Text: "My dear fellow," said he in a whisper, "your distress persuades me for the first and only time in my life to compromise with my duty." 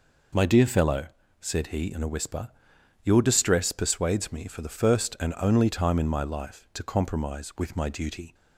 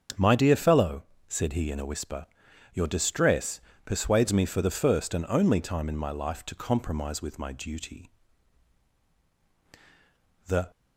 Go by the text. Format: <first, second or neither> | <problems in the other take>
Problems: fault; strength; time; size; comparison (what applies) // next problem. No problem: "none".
first | starts louder than the rest; until 1.4 s; 7 dB // pauses between "distress" and "persuades"; slight; at 3.6 s; 0.24 s long // goes on to say "The"; slight; from 10.4 s on; 0.24 s long